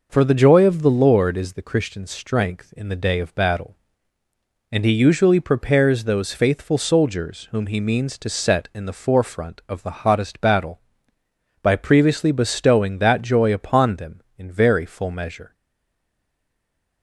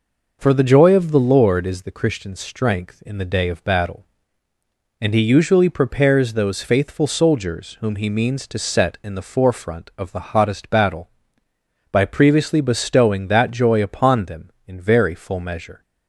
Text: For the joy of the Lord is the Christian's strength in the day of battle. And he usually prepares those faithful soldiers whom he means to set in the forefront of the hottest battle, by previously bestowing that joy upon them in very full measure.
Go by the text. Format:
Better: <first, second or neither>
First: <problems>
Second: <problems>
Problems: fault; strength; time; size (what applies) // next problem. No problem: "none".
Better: second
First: stays silent after the last word; noticeable; from 15.5 s on; 1.5 s long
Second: none